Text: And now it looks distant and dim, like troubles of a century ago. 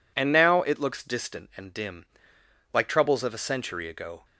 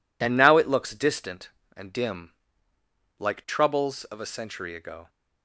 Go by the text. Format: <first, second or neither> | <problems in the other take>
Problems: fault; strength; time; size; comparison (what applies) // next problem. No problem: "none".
neither | none